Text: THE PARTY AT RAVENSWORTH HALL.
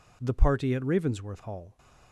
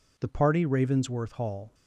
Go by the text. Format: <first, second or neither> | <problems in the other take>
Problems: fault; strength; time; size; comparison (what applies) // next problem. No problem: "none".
first | skips "AT"; at 0.6 s